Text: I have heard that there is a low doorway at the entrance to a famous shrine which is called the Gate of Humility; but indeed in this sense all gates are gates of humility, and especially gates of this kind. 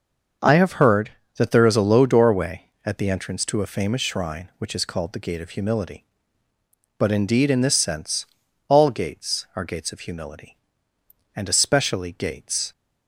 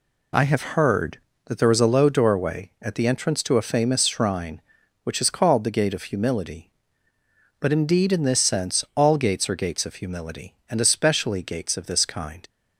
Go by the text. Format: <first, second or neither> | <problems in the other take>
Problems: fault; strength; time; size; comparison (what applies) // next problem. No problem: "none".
second | starts louder than the rest; until 1.6 s; 6.5 dB // pauses between "sense" and "all"; at 8.2 s; 0.44 s long // stops before "of this kind"; at 12.7 s